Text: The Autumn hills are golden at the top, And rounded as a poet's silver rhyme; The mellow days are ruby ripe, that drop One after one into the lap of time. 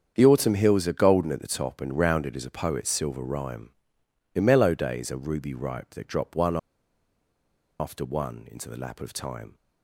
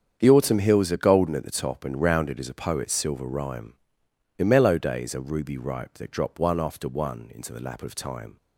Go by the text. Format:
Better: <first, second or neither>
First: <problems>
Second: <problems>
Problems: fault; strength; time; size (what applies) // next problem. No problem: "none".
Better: second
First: starts louder than the rest; strong; until 1.1 s; 8 dB // pauses between "One" and "after"; at 6.5 s; 1.2 s long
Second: starts louder than the rest; strong; until 1.2 s; 8 dB